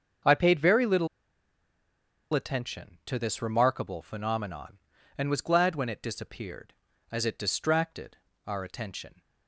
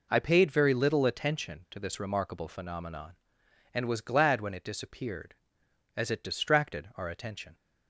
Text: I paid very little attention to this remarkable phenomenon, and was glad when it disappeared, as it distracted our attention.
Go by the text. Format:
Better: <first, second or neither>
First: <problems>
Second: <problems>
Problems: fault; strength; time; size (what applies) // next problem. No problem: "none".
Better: second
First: starts louder than the rest; until 2.5 s; 6.5 dB // pauses between "little" and "attention"; strong; at 1.0 s; 1.2 s long // pauses between "distracted" and "our"; slight; at 8.1 s; 0.30 s long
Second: none